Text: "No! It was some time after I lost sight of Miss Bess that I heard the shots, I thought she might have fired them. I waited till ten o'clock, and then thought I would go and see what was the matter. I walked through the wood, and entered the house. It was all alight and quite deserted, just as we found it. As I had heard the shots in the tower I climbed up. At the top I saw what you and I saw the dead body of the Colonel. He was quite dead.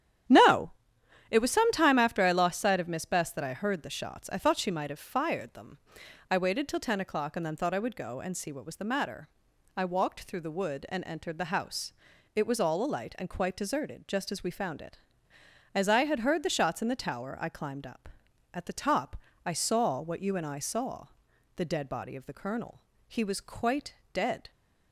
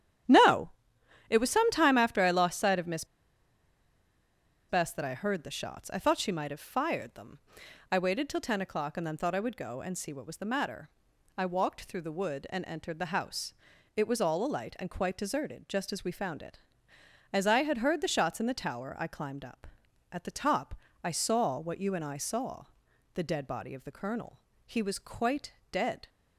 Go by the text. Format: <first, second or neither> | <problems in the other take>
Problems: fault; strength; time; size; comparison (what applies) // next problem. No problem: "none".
first | starts louder than the rest; strong; until 1.8 s; 10.5 dB; strong in the first // pauses between "Miss" and "Bess"; strong; at 3.0 s; 1.6 s long // pauses between "top" and "I"; slight; at 20.7 s; 0.30 s long; slight in the first // pauses between "saw" and "the"; noticeable; at 22.6 s; 0.50 s long; noticeable in the first // pauses between "quite" and "dead"; slight; at 25.5 s; 0.18 s long; slight in the first